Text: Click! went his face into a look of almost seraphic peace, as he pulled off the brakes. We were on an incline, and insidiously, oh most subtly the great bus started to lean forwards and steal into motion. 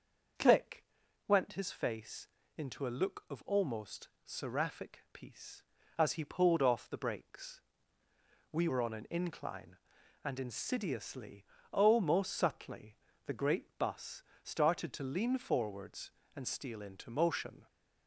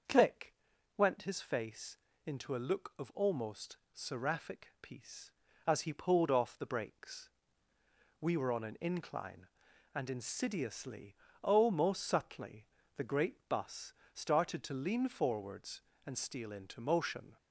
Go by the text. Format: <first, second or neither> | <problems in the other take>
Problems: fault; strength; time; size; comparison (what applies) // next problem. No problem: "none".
neither | starts louder than the rest; the same in both // pauses between "face" and "into"; slight; the same in both // pauses between "almost" and "seraphic"; slight; the same in both // pauses between "subtly" and "the"; slight; the same in both // pauses between "bus" and "started"; slight; the same in both